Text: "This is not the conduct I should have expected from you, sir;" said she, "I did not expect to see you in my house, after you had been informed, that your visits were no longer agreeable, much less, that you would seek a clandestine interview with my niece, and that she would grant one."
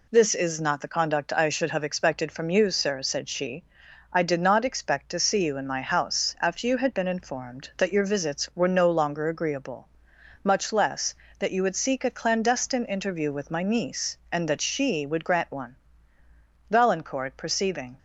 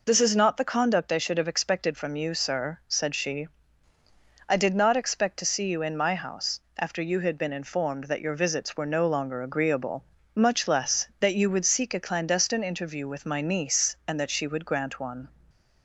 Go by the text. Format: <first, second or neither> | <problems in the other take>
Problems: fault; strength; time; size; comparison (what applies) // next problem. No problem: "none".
second | goes on to say "Valancourt perceiving"; noticeable; from 16.6 s on; 1.2 s long